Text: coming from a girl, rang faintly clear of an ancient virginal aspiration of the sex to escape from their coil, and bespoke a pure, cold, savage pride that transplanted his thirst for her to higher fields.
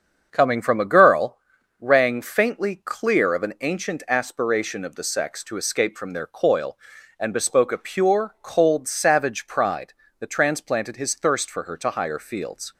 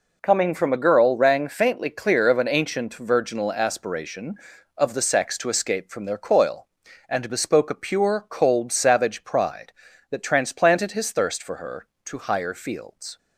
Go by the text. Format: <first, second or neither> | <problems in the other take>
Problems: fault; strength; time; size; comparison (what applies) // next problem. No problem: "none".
second | starts louder than the rest; until 1.3 s; 7 dB // skips "virginal"; at 4.0 s